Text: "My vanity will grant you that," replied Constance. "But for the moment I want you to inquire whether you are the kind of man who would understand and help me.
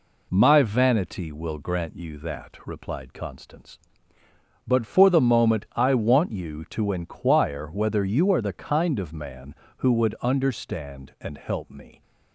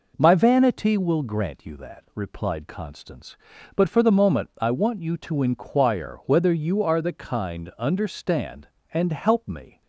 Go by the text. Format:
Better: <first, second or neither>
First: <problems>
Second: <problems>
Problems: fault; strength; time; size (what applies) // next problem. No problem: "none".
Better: first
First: none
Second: skips "of man who would"; at 7.7 s